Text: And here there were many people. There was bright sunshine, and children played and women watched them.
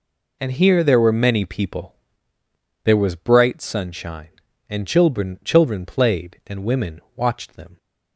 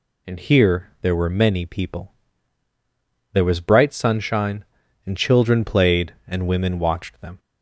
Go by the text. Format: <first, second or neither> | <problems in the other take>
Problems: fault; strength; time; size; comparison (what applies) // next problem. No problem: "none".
second | says "children" twice; at 5.4 s